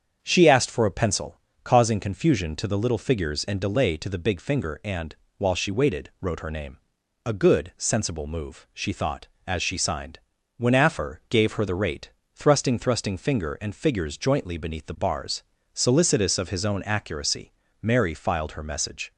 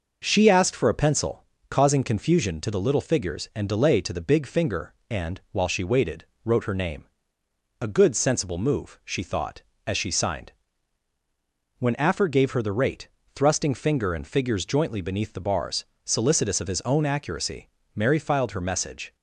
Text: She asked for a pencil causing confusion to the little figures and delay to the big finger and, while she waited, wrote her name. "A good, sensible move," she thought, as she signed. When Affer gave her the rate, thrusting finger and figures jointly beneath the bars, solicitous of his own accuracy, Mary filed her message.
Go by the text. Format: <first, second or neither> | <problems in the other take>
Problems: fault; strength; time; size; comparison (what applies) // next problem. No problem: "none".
second | starts louder than the rest; strong; until 1.2 s; 7.5 dB // pauses between "pencil" and "causing"; slight; at 1.3 s; 0.24 s long; slight in the second // says "thrusting" twice; at 12.7 s